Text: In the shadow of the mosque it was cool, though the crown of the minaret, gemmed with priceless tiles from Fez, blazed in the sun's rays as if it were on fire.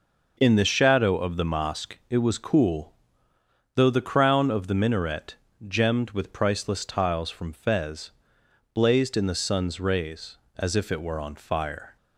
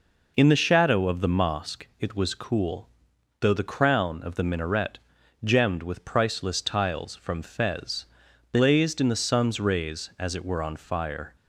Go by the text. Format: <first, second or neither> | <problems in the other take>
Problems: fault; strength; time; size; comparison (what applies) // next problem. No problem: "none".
first | skips "if"; at 10.3 s